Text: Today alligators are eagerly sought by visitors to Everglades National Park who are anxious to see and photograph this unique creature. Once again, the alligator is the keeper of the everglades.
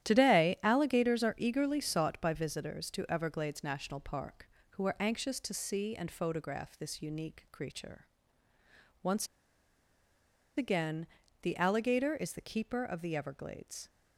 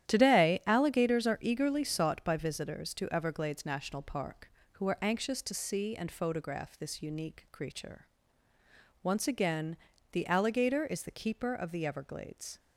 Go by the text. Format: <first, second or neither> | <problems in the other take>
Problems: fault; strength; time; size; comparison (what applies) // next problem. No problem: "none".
second | starts louder than the rest; strong; until 1.0 s; 11.5 dB; strong in the second // pauses between "Once" and "again"; strong; at 9.2 s; 1.3 s long